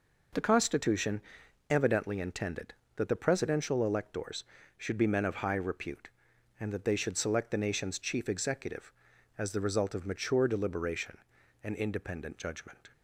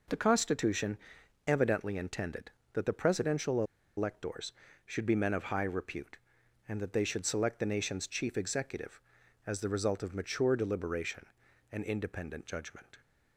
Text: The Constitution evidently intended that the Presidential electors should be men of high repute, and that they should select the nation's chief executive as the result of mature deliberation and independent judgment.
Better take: first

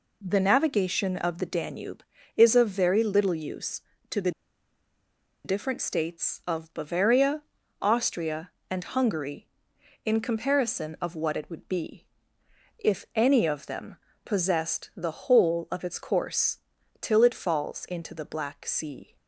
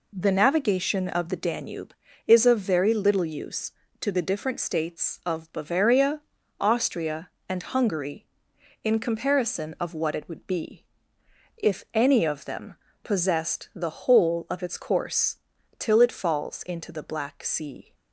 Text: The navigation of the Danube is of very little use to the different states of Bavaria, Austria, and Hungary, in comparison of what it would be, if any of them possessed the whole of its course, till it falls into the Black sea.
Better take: second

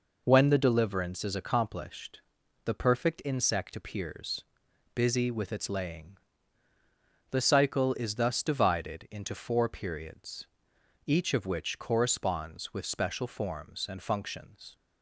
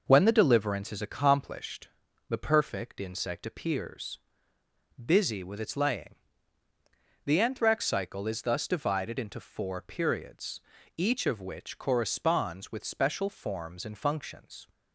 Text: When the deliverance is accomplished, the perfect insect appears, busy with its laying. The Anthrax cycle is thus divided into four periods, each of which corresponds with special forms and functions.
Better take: second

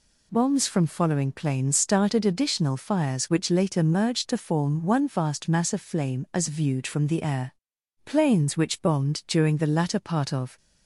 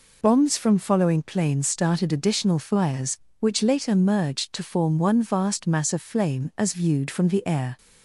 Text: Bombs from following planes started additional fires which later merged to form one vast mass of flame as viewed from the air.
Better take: second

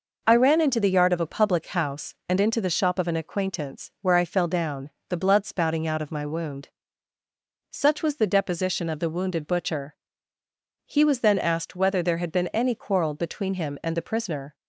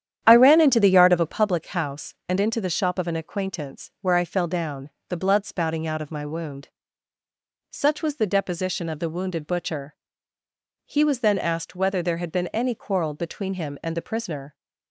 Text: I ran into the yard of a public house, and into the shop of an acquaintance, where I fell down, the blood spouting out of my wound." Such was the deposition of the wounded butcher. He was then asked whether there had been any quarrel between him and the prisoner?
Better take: first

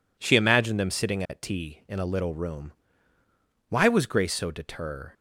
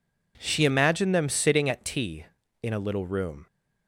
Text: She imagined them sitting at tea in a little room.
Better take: second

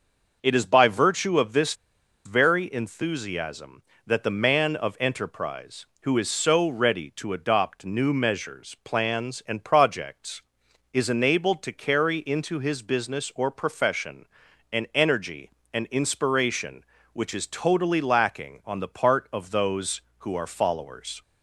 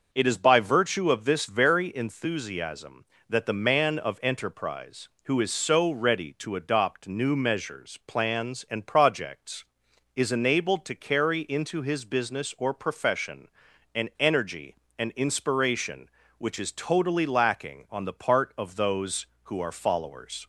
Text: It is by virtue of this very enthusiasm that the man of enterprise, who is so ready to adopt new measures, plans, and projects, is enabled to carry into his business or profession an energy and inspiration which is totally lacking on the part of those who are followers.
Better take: second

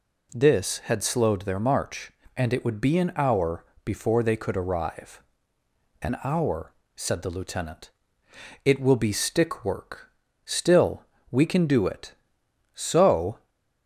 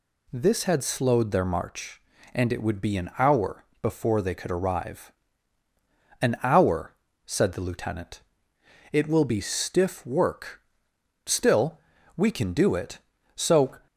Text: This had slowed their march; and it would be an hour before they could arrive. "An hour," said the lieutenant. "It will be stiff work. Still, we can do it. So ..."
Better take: second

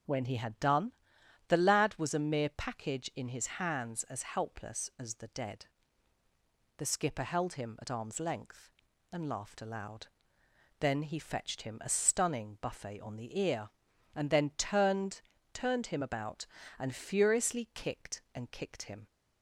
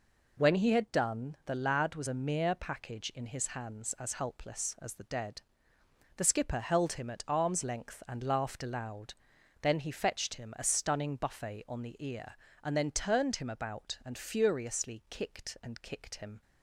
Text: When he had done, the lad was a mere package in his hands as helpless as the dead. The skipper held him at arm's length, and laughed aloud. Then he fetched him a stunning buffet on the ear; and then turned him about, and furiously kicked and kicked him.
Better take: second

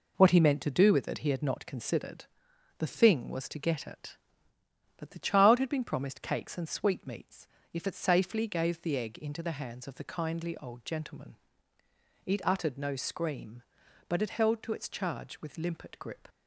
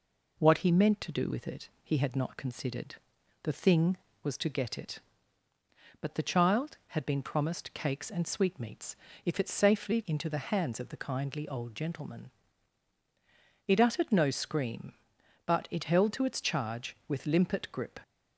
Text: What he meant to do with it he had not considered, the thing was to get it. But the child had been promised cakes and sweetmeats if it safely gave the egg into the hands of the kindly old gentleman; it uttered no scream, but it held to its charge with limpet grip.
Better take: first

